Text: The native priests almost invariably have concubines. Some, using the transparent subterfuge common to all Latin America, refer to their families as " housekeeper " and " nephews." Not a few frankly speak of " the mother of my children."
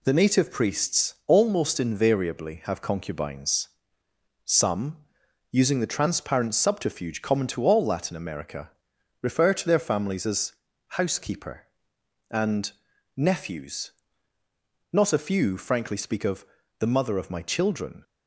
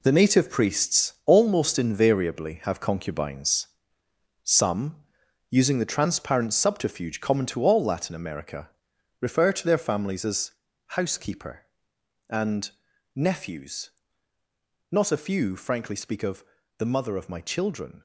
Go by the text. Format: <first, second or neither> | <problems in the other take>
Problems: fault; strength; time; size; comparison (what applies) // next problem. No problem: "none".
first | gets quieter; strong; throughout; 15.5 dB